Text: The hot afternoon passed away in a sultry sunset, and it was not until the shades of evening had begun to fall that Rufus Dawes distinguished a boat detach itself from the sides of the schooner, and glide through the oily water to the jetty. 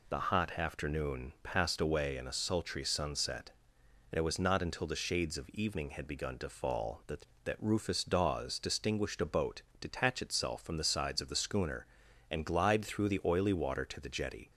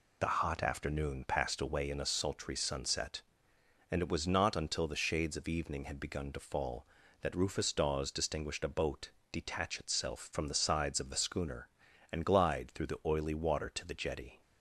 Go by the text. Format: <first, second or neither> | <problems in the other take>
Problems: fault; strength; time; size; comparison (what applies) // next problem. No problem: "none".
second | says "that" twice; at 7.4 s // pauses between "boat" and "detach"; slight; at 9.6 s; 0.18 s long; slight in the second